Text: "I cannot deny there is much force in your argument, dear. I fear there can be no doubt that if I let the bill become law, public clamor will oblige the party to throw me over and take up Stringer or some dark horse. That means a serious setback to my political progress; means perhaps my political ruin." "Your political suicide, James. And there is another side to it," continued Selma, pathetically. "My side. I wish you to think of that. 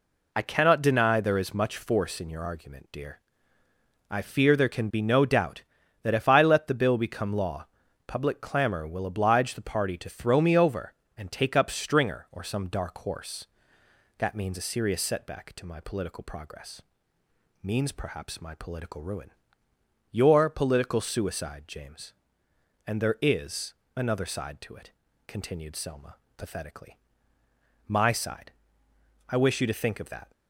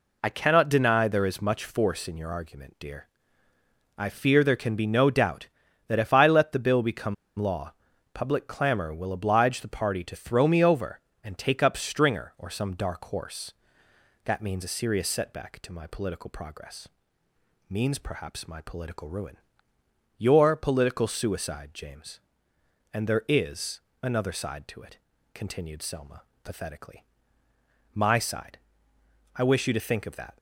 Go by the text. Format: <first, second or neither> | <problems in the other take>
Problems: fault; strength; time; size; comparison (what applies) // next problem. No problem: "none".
first | pauses between "become" and "law"; slight; at 7.1 s; 0.24 s long // pauses between "is" and "another"; slight; at 23.7 s; 0.22 s long; slight in the first